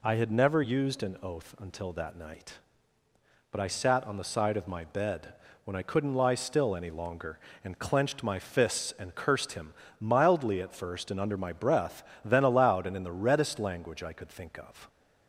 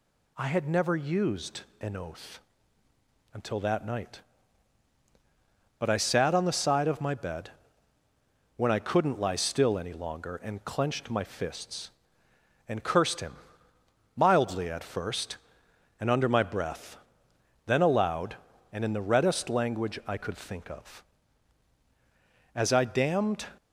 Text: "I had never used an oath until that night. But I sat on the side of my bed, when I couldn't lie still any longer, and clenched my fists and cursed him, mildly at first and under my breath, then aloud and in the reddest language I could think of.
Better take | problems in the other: first | pauses between "used" and "an"; slight; at 1.6 s; 0.18 s long // pauses between "oath" and "until"; noticeable; at 2.3 s; 0.94 s long // goes on to say "As I damned"; noticeable; from 22.5 s on; 0.92 s long

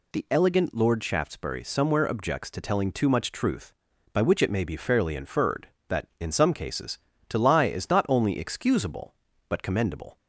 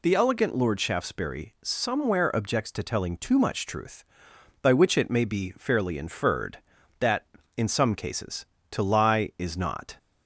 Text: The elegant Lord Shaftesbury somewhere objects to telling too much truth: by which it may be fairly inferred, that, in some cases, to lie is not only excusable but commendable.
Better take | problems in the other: first | stops before "only excusable but commendable"; at 9.9 s

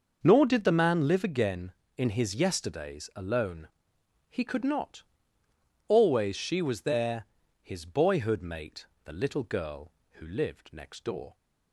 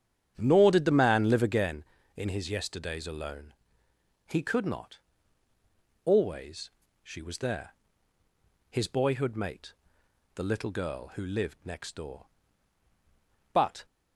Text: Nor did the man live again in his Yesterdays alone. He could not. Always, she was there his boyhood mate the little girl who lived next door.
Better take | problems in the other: first | starts louder than the rest; strong; until 1.3 s; 8.5 dB; noticeable in the first // pauses between "there" and "his"; at 7.7 s; 1.0 s long; also in the first // pauses between "mate" and "the"; noticeable; at 9.7 s; 0.62 s long; slight in the first // goes on to say "But"; slight; from 13.5 s on; 0.32 s long

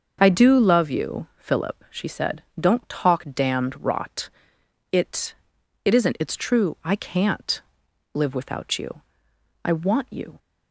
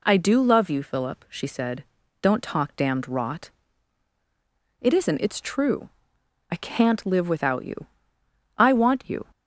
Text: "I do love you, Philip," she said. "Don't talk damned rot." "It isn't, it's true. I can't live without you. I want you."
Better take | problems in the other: second | starts louder than the rest; until 1.2 s; 6.5 dB // says "It" twice; at 5.8 s // pauses between "can't" and "live"; noticeable; at 7.6 s; 0.54 s long

